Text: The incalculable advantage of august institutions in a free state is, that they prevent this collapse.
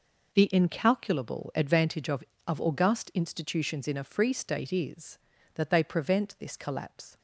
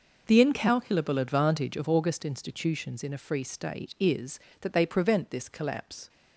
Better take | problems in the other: second | says "of" twice; at 2.4 s

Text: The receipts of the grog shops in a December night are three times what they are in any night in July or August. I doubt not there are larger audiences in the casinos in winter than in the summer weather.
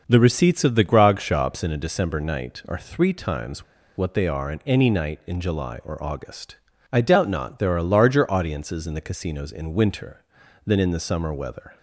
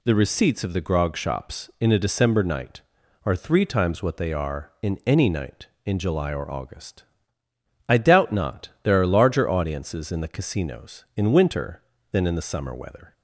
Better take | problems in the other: second | pauses between "times" and "what"; slight; at 3.6 s; 0.32 s long

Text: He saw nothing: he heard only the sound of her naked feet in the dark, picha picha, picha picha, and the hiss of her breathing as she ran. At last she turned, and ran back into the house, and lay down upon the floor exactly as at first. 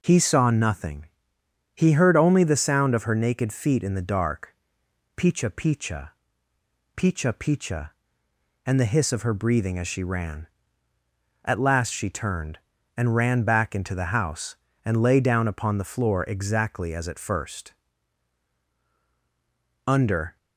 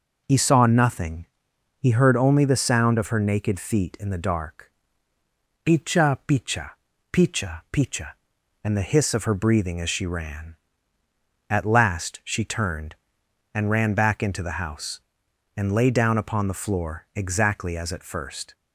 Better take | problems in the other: second | goes on to say "Under"; from 19.8 s on; 0.52 s long

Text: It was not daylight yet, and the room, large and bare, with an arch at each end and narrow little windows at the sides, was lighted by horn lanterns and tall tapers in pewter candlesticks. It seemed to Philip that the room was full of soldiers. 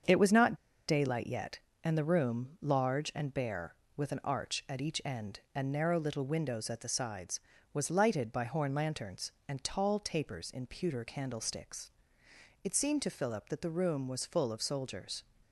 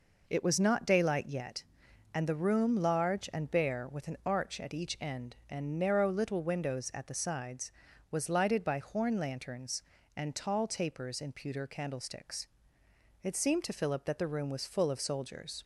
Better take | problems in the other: second | starts louder than the rest; until 1.4 s; 7 dB // pauses between "not" and "daylight"; slight; at 0.5 s; 0.33 s long

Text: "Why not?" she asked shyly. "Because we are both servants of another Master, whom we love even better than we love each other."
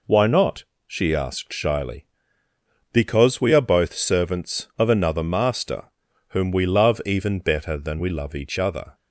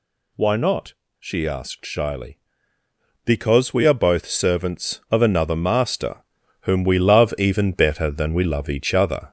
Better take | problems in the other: first | gets louder; throughout; 3.5 dB

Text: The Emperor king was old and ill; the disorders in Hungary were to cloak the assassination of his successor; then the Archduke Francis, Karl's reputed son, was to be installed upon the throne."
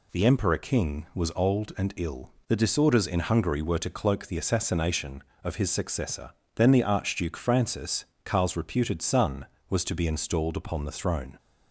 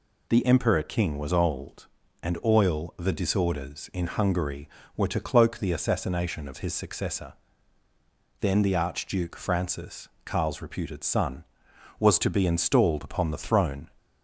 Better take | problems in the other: first | says "oil" for "ill"; at 2.4 s

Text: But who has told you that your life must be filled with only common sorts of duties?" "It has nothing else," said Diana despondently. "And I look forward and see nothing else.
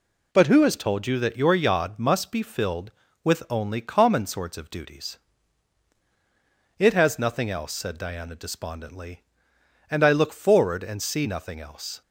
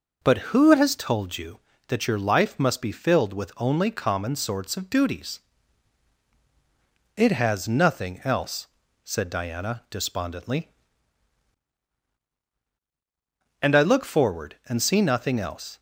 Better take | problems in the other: second | says "yod" for "life"; at 1.5 s

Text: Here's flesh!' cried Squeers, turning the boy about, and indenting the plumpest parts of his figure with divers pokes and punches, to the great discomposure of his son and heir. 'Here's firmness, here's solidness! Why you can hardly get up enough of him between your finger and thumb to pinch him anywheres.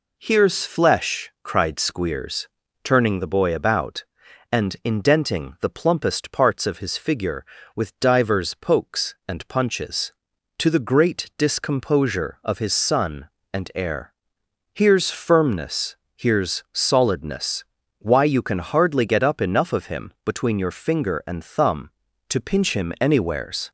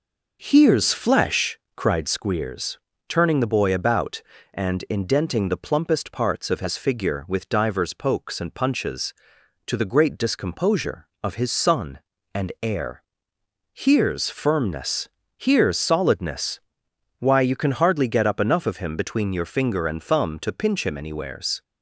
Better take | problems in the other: first | starts louder than the rest; noticeable; until 2.3 s; 6 dB

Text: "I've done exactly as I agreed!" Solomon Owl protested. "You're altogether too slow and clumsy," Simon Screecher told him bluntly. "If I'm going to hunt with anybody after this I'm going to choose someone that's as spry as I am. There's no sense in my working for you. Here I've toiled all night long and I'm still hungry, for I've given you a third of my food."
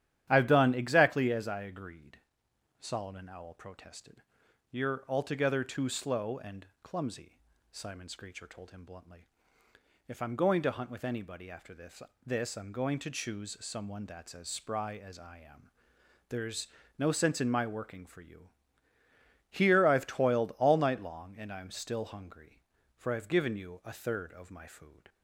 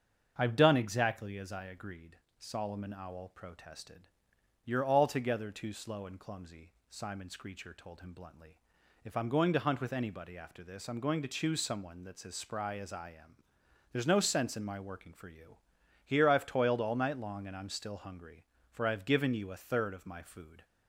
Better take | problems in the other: second | starts louder than the rest; strong; until 1.2 s; 11 dB; also in the second // pauses between "and" and "clumsy"; slight; at 6.6 s; 0.16 s long // says "this" twice; at 12.2 s // pauses between "There's" and "no"; slight; at 16.6 s; 0.32 s long

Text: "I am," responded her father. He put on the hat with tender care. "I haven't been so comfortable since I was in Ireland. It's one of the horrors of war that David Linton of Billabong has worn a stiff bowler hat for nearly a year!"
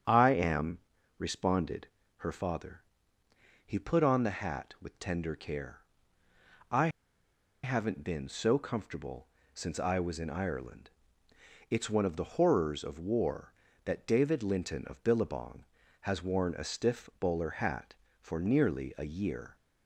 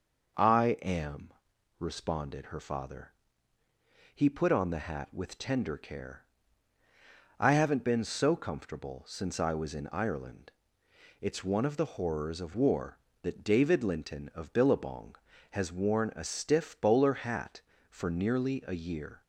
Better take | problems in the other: second | starts louder than the rest; strong; until 1.4 s; 8 dB // pauses between "responded" and "her"; slight; at 1.8 s; 0.30 s long // pauses between "I" and "haven't"; noticeable; at 6.8 s; 0.74 s long // pauses between "comfortable" and "since"; slight; at 9.2 s; 0.28 s long

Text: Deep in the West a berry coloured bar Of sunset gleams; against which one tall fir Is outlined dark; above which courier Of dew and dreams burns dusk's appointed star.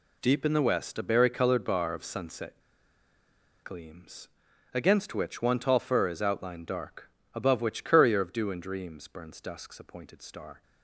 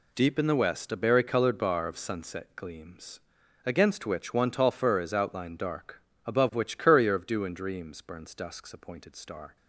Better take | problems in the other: second | pauses between "sunset" and "gleams"; at 2.5 s; 1.0 s long

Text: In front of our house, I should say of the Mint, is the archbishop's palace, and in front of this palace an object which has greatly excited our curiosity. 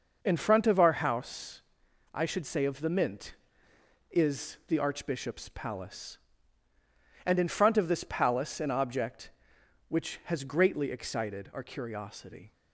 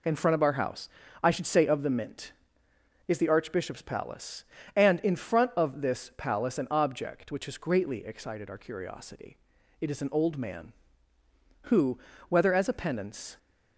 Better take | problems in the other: first | goes on to say "It is an old man who whether as a penance"; strong; from 9.7 s on; 3.5 s long

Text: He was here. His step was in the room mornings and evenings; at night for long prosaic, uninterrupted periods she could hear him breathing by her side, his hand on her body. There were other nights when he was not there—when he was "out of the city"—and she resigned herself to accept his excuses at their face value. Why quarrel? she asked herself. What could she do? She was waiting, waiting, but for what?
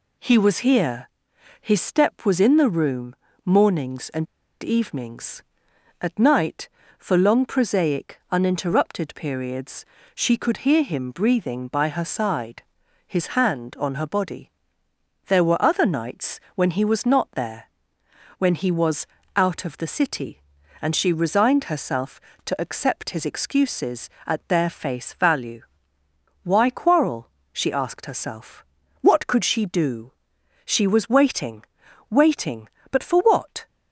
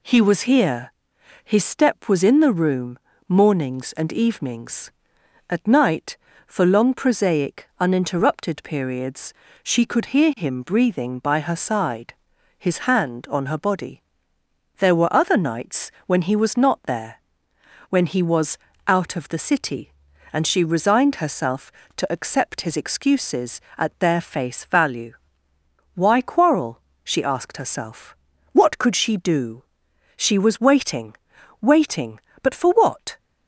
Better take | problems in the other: second | pauses between "room" and "mornings"; slight; at 3.1 s; 0.30 s long; slight in the second // pauses between "and" and "evenings"; at 4.2 s; 0.36 s long // pauses between "periods" and "she"; slight; at 9.8 s; 0.30 s long; slight in the second // pauses between "nights" and "when"; slight; at 16.3 s; 0.16 s long; slight in the second // pauses between "was" and "out"; slight; at 19.0 s; 0.28 s long; slight in the second

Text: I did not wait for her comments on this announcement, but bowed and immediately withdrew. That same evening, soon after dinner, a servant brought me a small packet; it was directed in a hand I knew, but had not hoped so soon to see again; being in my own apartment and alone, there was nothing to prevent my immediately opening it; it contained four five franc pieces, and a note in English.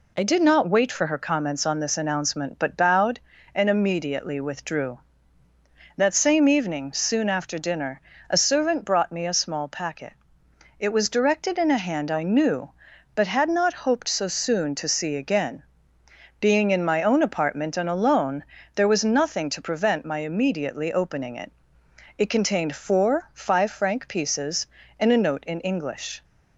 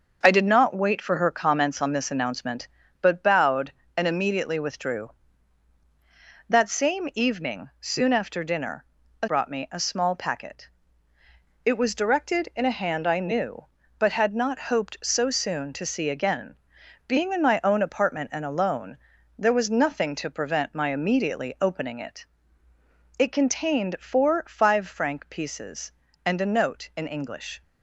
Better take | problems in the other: first | starts louder than the rest; until 1.2 s; 6.5 dB // skips "servant"; at 9.2 s

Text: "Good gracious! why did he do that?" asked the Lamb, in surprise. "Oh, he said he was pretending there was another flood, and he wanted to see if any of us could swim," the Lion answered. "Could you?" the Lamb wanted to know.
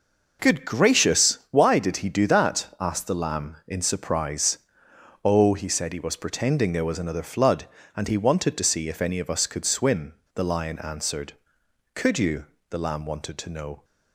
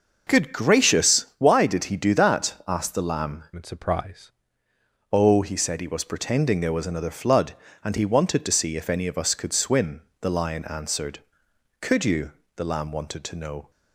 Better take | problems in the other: first | changes voice from "in" to "surprise"; from 3.5 to 4.3 s; 0.8 s long

